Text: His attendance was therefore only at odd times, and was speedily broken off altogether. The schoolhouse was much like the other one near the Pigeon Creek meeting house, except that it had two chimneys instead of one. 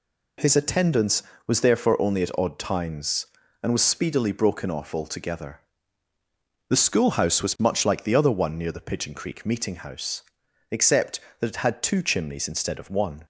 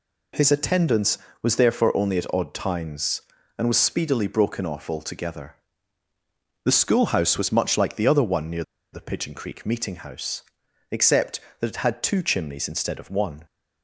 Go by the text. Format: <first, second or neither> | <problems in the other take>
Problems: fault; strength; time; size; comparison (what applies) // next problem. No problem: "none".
first | pauses between "near" and "the"; slight; at 8.6 s; 0.28 s long